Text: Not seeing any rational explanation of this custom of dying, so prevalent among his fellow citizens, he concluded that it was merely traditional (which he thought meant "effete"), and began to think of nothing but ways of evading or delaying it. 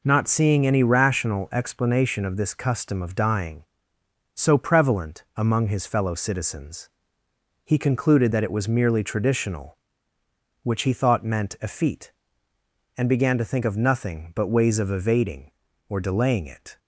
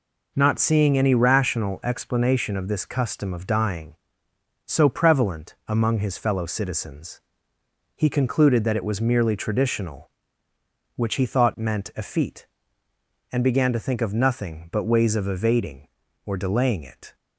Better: neither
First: none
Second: none

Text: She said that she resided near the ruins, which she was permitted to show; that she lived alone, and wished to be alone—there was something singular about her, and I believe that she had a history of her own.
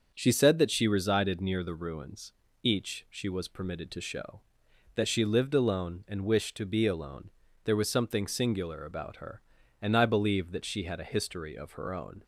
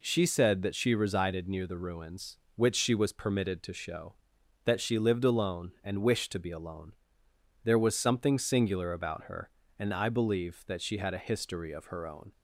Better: second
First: starts louder than the rest; until 1.1 s; 6.5 dB // says "each" for "which"; at 2.6 s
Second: none

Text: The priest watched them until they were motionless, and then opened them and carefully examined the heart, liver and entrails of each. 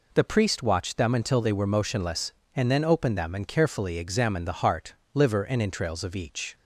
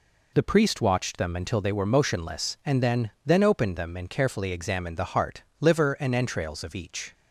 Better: first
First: none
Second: says "then" twice; at 3.2 s

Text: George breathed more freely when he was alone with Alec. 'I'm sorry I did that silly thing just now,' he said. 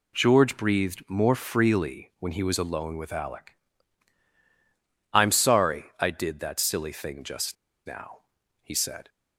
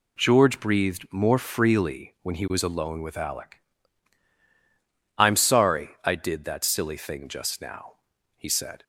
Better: second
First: pauses between "just" and "now"; slight; at 7.5 s; 0.31 s long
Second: none

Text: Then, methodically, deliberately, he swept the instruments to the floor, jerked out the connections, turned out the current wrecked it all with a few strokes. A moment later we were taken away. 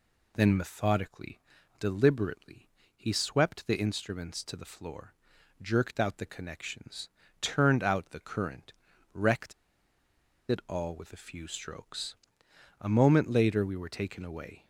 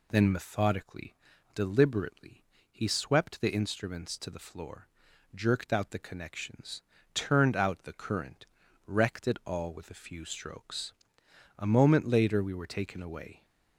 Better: second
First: pauses between "current" and "wrecked"; at 8.7 s; 0.40 s long // pauses between "wrecked" and "it"; noticeable; at 9.5 s; 0.95 s long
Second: pauses between "current" and "wrecked"; at 8.4 s; 0.40 s long

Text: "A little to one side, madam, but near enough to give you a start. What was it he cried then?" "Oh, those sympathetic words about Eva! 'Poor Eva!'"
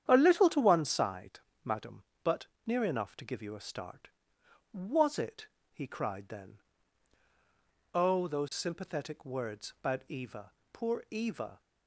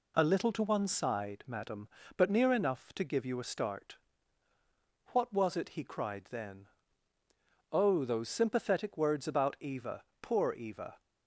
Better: second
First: starts louder than the rest; strong; until 1.1 s; 9 dB // pauses between "but" and "near"; slight; at 2.4 s; 0.18 s long // skips "What"; at 4.4 s // pauses between "it" and "he"; slight; at 5.4 s; 0.24 s long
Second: none

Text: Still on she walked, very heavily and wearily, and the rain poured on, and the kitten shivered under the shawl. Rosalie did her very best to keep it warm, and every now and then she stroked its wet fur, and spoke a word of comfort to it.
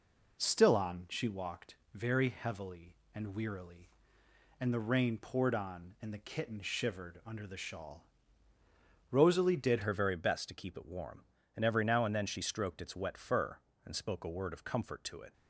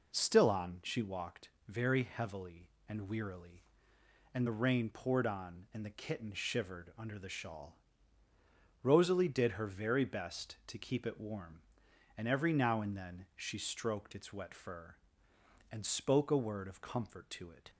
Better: second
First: changes voice at "her"; from 9.8 s on; 5.5 s long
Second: none

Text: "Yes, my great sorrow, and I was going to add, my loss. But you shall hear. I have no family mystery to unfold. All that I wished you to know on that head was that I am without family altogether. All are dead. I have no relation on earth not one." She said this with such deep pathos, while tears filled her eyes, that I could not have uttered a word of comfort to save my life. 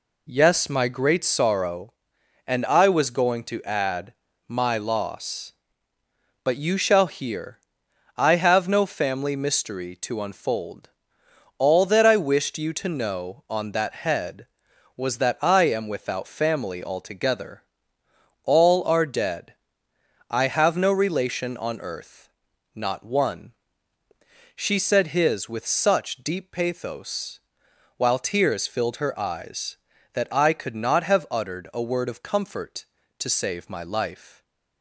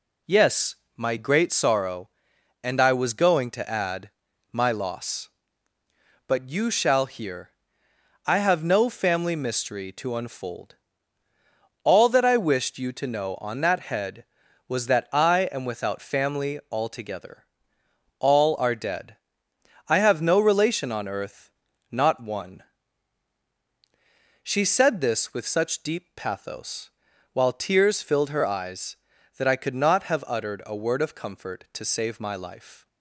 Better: second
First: pauses between "earth" and "not"; noticeable; at 22.2 s; 0.48 s long // says "his" for "this"; at 25.0 s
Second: pauses between "earth" and "not"; at 21.4 s; 0.42 s long

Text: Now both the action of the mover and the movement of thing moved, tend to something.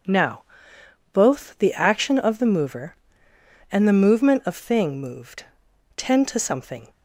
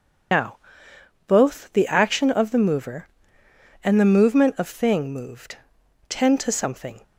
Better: first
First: pauses between "Now" and "both"; noticeable; at 0.4 s; 0.72 s long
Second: loses the start of "Now"; at 0.3 s; 105 ms // pauses between "Now" and "both"; noticeable; at 0.5 s; 0.72 s long

